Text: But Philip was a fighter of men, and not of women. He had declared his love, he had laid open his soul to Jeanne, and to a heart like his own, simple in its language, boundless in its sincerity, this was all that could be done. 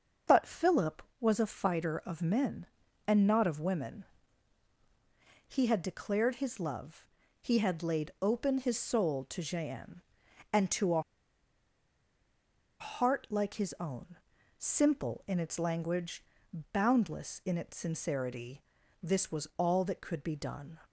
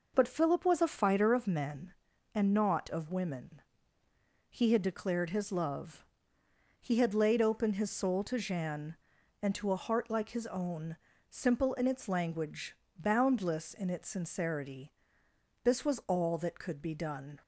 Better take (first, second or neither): second